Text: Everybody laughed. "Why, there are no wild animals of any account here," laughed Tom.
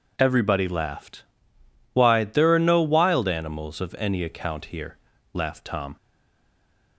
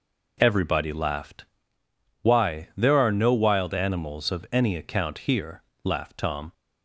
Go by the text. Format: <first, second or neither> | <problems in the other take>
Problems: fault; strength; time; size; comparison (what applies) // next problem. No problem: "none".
second | stays silent after the last word; from 5.9 s on; 1.0 s long